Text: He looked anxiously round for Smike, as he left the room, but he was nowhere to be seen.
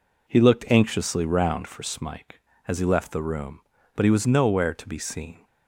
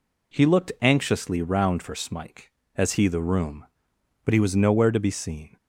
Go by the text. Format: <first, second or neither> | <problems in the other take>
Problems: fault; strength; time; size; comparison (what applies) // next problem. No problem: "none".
first | skips "left"; at 3.0 s